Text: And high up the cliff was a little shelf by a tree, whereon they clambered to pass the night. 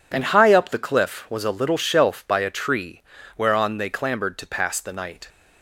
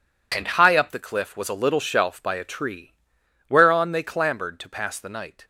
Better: neither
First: none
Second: none

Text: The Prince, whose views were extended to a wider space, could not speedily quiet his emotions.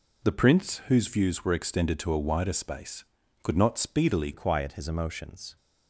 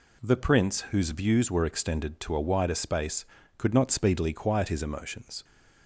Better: second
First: changes voice at "quiet"; from 4.3 s on; 1.2 s long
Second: none

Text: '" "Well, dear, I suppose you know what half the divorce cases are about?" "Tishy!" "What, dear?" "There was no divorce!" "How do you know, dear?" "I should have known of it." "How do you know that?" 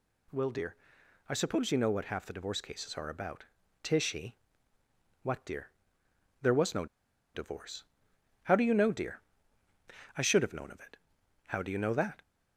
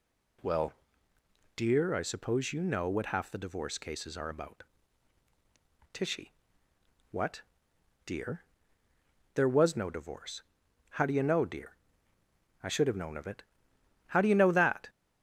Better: second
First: pauses between "no" and "divorce"; noticeable; at 6.8 s; 0.49 s long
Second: none

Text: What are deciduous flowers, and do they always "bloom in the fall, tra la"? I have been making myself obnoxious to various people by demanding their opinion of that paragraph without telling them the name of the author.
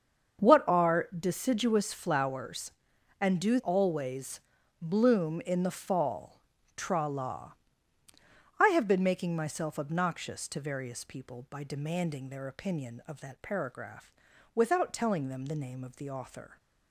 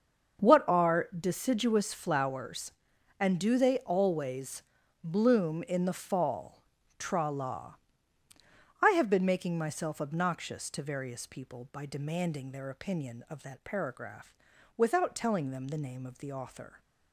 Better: second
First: starts louder than the rest; until 1.5 s; 7 dB // skips "they"; at 3.5 s // pauses between "always" and "bloom"; at 4.4 s; 0.40 s long // pauses between "paragraph" and "without"; at 14.1 s; 0.44 s long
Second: starts louder than the rest; until 1.5 s; 6.5 dB // pauses between "always" and "bloom"; at 4.6 s; 0.40 s long // pauses between "paragraph" and "without"; at 14.3 s; 0.44 s long

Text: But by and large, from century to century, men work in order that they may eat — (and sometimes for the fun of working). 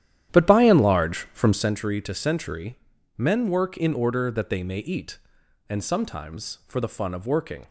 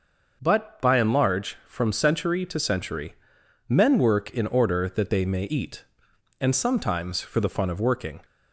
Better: second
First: starts louder than the rest; strong; until 1.8 s; 11 dB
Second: none

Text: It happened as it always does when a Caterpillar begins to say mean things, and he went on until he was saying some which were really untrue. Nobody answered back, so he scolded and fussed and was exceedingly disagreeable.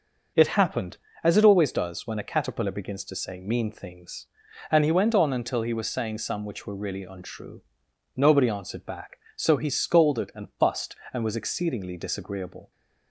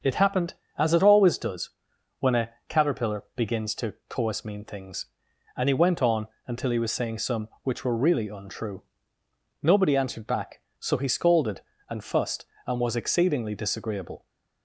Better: first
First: none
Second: starts louder than the rest; until 1.2 s; 6.5 dB // pauses between "does" and "when"; noticeable; at 1.6 s; 0.50 s long // pauses between "a" and "Caterpillar"; slight; at 2.4 s; 0.18 s long // says "coas" for "say"; at 4.0 s // pauses between "on" and "until"; slight; at 6.2 s; 0.18 s long

